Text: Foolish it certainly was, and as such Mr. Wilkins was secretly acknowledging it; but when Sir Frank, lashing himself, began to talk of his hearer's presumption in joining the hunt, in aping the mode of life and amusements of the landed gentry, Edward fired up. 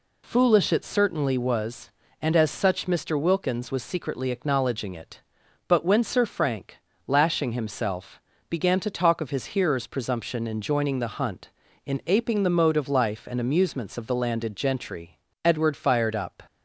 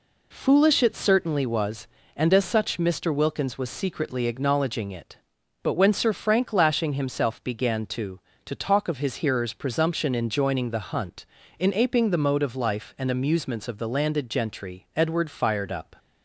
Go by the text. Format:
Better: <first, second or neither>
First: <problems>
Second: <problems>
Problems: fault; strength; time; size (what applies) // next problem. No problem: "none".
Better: first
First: none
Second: says "to" twice; at 8.4 s